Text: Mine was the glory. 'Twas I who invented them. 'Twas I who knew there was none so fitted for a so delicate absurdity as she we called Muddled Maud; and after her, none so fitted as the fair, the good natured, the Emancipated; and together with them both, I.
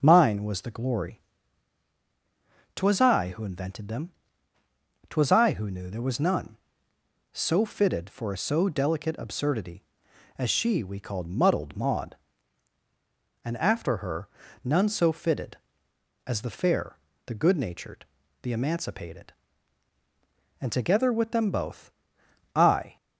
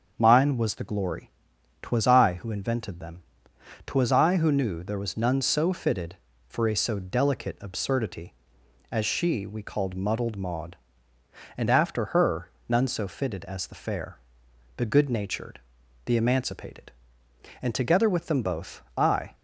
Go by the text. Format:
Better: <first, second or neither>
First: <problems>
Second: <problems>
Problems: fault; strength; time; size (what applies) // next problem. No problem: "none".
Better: neither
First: starts louder than the rest; until 1.0 s; 7 dB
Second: starts louder than the rest; until 1.1 s; 7 dB